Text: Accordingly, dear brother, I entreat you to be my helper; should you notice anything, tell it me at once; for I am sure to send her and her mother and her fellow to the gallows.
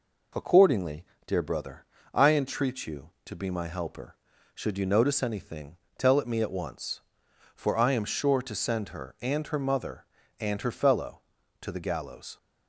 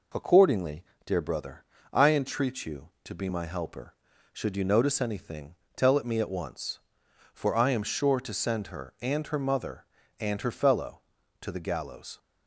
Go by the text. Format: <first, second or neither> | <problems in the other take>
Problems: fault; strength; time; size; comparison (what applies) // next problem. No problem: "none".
neither | none